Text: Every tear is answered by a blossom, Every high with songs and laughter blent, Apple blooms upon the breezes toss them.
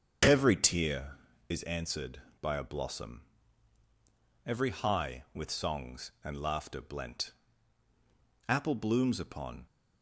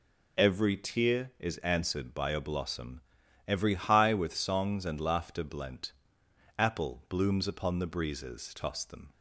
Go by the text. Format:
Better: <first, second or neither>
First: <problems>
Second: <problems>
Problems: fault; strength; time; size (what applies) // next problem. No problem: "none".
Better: second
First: starts louder than the rest; strong; until 1.5 s; 7.5 dB // stops before "the breezes toss them"; at 9.6 s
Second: none